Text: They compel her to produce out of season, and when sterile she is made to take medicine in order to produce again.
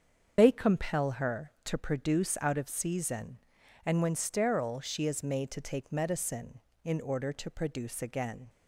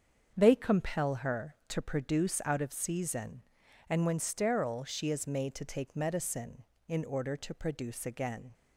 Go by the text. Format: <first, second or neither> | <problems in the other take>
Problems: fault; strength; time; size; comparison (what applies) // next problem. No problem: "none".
second | loses the start of "They"; at 0.3 s; 70 ms // starts louder than the rest; until 1.3 s; 7 dB; strong in the second